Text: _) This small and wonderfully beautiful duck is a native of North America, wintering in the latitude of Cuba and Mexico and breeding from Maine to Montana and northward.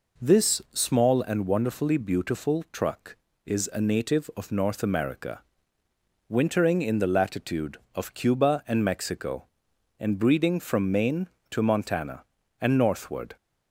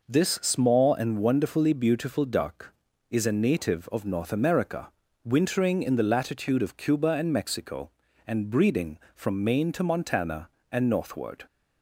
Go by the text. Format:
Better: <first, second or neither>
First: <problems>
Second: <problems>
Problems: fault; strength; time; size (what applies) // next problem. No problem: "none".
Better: second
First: says "truck" for "duck"; at 2.7 s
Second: none